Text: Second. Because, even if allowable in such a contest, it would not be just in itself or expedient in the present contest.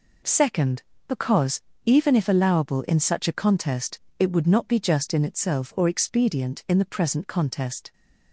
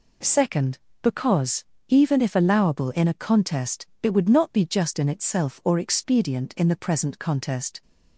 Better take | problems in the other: first | skips "such"; at 3.0 s

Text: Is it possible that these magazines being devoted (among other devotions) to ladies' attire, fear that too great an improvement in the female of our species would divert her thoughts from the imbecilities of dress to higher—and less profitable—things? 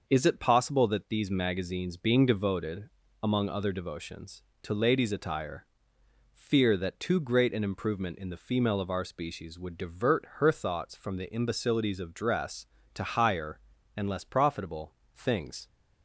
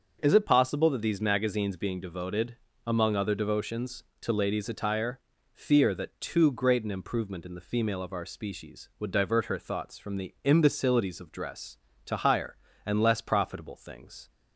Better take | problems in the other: neither | starts louder than the rest; the same in both

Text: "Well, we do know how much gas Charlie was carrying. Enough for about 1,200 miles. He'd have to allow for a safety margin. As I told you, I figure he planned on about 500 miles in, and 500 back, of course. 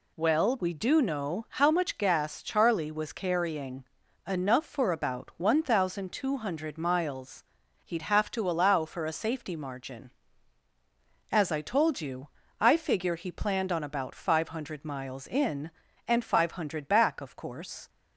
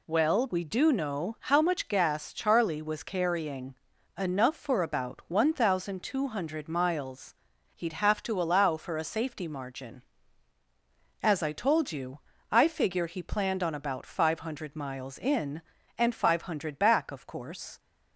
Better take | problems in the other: neither | none

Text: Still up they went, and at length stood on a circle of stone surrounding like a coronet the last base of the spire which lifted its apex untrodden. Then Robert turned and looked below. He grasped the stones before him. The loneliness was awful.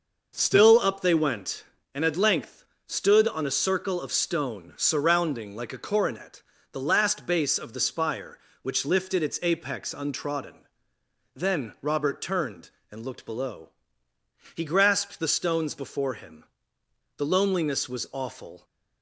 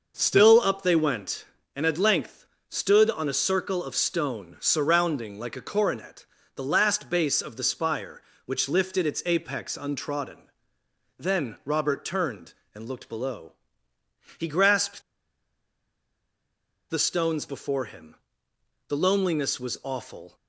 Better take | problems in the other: first | pauses between "length" and "stood"; slight; at 2.4 s; 0.24 s long; slight in the first // pauses between "coronet" and "the"; slight; at 6.2 s; 0.32 s long; slight in the first // pauses between "grasped" and "the"; strong; at 15.0 s; 1.8 s long

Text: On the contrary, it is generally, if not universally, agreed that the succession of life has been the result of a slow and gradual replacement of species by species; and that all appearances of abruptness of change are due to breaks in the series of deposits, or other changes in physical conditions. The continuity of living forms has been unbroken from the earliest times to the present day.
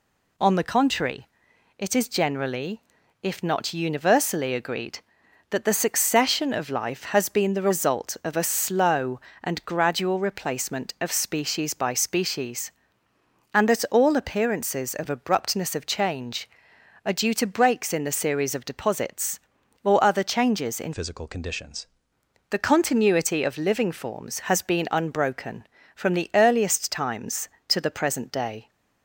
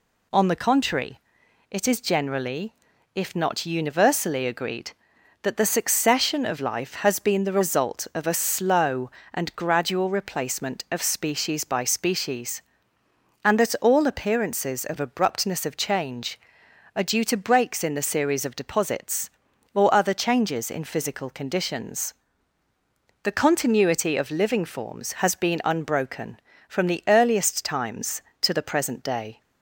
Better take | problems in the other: second | changes voice from "physical" to "conditions"; from 20.9 to 21.8 s; 0.9 s long

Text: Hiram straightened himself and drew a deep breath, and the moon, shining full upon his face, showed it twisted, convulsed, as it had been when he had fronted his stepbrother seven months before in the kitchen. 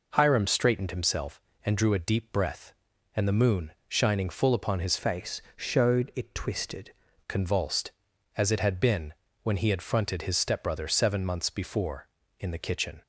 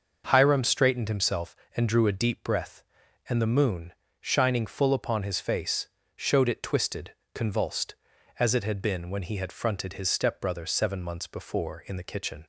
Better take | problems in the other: second | changes voice from "face" to "twisted"; from 4.9 to 6.9 s; 2.0 s long // pauses between "been" and "when"; slight; at 9.1 s; 0.30 s long

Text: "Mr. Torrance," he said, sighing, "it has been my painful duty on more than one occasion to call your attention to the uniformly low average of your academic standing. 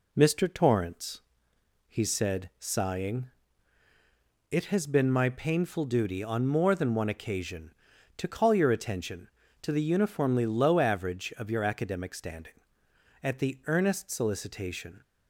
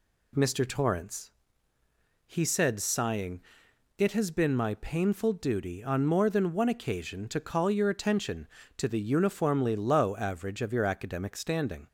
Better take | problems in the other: second | goes on to say "At the earnest solicitation"; strong; from 13.2 s on; 1.8 s long

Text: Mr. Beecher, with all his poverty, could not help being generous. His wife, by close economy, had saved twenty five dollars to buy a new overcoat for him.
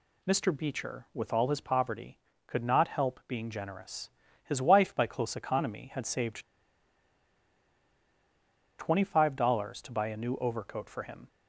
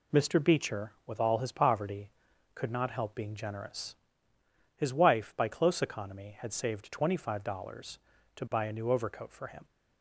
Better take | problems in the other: second | pauses between "saved" and "twenty"; strong; at 6.4 s; 2.3 s long

